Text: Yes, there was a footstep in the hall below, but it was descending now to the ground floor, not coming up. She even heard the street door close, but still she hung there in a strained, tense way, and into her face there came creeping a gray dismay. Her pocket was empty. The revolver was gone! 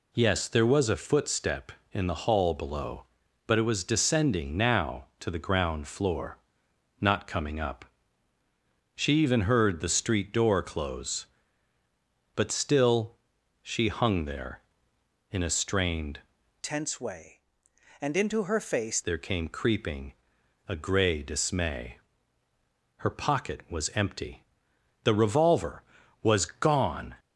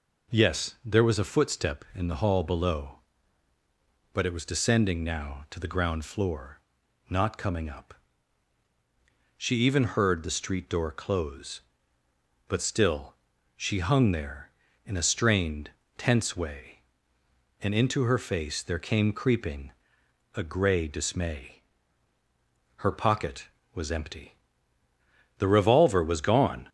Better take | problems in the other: second | pauses between "still" and "she"; noticeable; at 13.1 s; 0.46 s long; also in the second // changes voice from "tense" to "face"; from 16.6 to 19.0 s; 2.4 s long // pauses between "creeping" and "a"; noticeable; at 20.1 s; 0.54 s long; noticeable in the second

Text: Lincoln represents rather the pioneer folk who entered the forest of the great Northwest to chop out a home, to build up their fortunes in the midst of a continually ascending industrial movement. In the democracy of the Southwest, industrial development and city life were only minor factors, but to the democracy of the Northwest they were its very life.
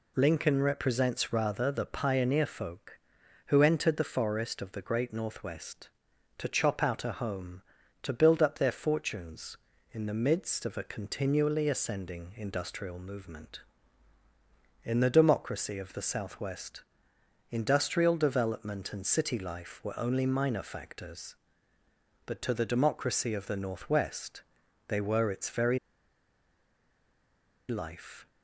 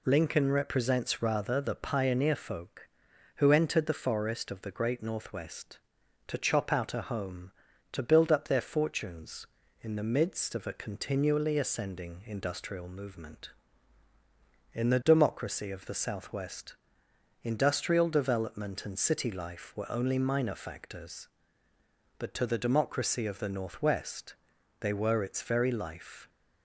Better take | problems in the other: second | pauses between "Northwest" and "they"; noticeable; at 24.4 s; 0.46 s long; noticeable in the second // pauses between "very" and "life"; strong; at 25.7 s; 1.9 s long

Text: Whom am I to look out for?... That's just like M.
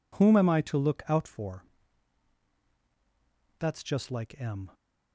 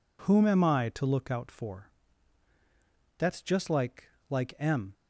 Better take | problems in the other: first | says "like" twice; at 4.2 s

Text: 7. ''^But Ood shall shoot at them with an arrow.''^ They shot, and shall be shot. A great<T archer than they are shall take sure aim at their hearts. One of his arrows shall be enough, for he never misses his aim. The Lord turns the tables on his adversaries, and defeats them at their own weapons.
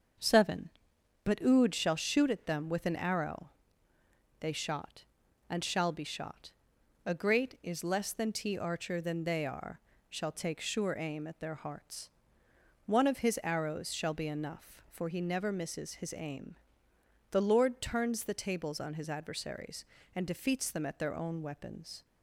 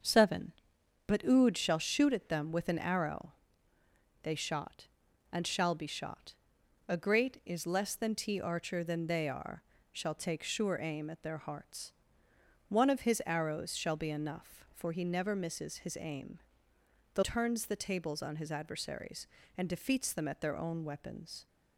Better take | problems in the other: first | starts louder than the rest; until 1.5 s; 6.5 dB; also in the first // pauses between "are" and "shall"; slight; at 9.6 s; 0.30 s long; slight in the first // skips "Lord"; at 17.2 s

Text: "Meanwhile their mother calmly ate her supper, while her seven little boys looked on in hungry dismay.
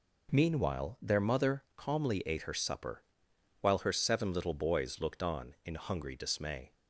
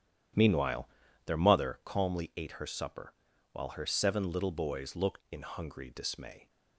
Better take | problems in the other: first | starts louder than the rest; strong; until 1.7 s; 10.5 dB // pauses between "Meanwhile" and "their"; at 0.8 s; 0.38 s long // skips "on"; at 5.2 s

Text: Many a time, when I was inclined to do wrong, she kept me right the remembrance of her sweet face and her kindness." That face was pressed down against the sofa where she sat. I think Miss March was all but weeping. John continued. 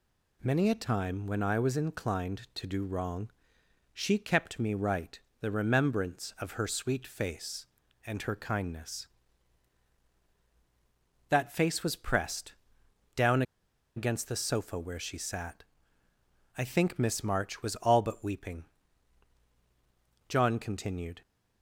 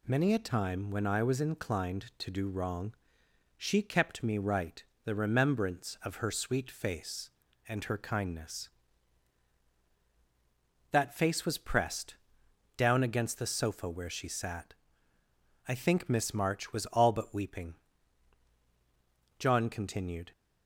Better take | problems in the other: second | pauses between "right" and "the"; slight; at 5.2 s; 0.22 s long; slight in the second // pauses between "pressed" and "down"; noticeable; at 12.5 s; 0.62 s long; noticeable in the second // pauses between "down" and "against"; noticeable; at 13.4 s; 0.54 s long

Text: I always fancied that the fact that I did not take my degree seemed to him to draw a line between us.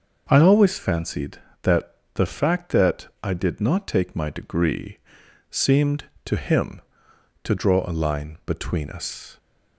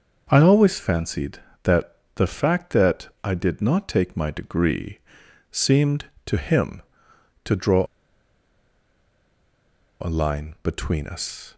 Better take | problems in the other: first | pauses between "that" and "the"; slight; at 1.9 s; 0.20 s long; slight in the first // pauses between "that" and "I"; slight; at 3.0 s; 0.16 s long; slight in the first // pauses between "degree" and "seemed"; noticeable; at 4.9 s; 0.52 s long; noticeable in the first // pauses between "draw" and "a"; strong; at 7.8 s; 2.1 s long

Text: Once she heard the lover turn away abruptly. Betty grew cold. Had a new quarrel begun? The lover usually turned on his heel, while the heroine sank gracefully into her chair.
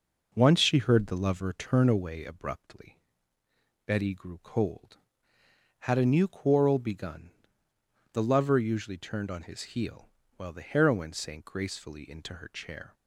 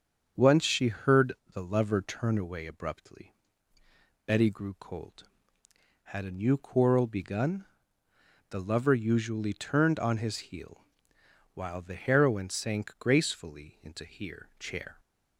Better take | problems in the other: first | starts louder than the rest; strong; until 1.6 s; 7.5 dB // pauses between "heard" and "the"; slight; at 1.3 s; 0.22 s long // says "here" for "her"; at 14.0 s

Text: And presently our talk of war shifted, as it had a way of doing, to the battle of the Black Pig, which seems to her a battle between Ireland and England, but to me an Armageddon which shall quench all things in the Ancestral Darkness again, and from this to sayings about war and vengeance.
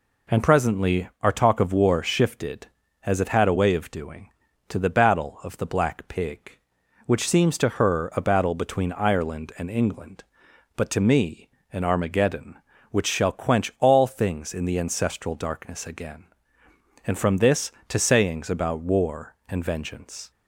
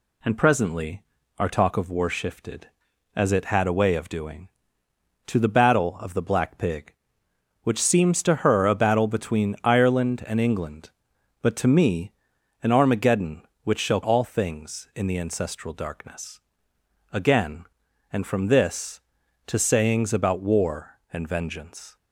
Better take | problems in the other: first | pauses between "presently" and "our"; slight; at 1.0 s; 0.36 s long // pauses between "me" and "an"; noticeable; at 12.1 s; 0.50 s long; slight in the first // skips "quench"; at 14.0 s // pauses between "Darkness" and "again"; noticeable; at 16.4 s; 0.72 s long

